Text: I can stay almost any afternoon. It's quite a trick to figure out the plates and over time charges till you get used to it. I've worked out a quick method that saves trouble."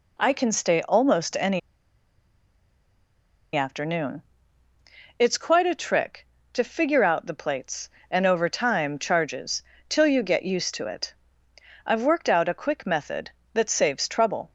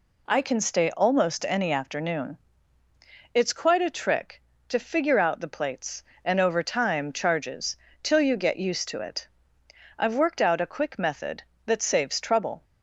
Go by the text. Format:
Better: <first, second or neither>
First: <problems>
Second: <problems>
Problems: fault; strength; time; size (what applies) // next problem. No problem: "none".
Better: second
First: pauses between "any" and "afternoon"; strong; at 1.5 s; 1.9 s long // pauses between "charges" and "till"; slight; at 9.6 s; 0.24 s long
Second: pauses between "charges" and "till"; slight; at 7.7 s; 0.24 s long